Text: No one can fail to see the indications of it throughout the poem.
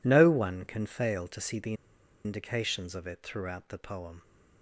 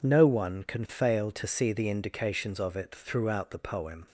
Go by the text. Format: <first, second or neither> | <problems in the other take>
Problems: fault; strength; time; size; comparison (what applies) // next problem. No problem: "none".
second | pauses between "the" and "indications"; noticeable; at 1.7 s; 0.51 s long